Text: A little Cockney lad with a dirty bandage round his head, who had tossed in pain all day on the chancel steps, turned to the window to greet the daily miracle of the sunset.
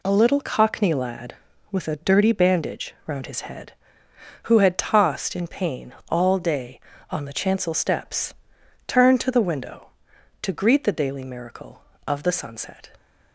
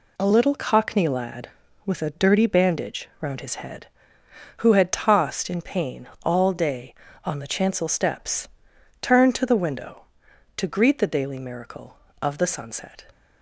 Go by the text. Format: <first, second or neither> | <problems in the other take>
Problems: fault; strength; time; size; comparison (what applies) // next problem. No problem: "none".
neither | pauses between "pain" and "all"; slight; the same in both